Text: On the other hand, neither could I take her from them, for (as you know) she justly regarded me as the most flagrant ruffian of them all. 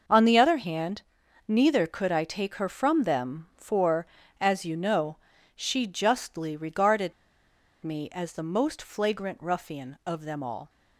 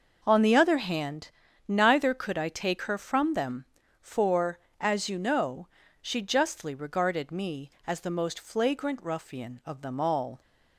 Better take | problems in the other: second | starts louder than the rest; noticeable; until 1.5 s; 6 dB // pauses between "regarded" and "me"; noticeable; at 7.1 s; 0.72 s long

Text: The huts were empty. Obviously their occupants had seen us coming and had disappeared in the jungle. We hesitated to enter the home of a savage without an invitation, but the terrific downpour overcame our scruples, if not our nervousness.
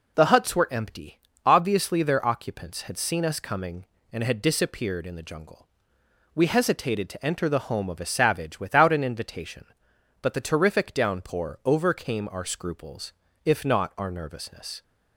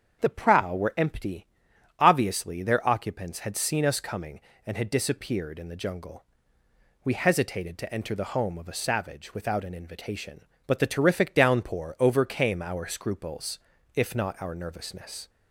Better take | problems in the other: first | starts louder than the rest; strong; until 1.2 s; 7 dB // says "prow" for "huts"; at 0.2 s

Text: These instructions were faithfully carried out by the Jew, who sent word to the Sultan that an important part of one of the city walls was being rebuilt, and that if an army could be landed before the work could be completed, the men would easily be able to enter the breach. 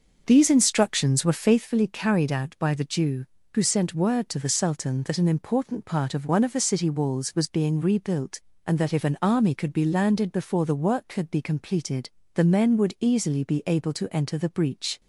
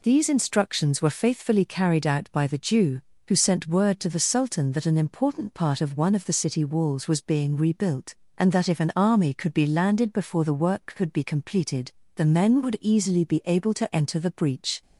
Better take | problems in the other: second | starts louder than the rest; until 1.7 s; 6 dB

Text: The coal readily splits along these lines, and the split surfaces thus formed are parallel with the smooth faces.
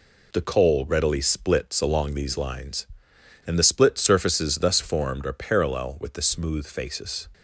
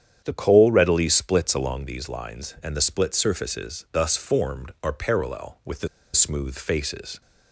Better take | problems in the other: first | starts louder than the rest; strong; until 1.2 s; 9 dB // pauses between "the" and "smooth"; slight; at 5.8 s; 0.26 s long

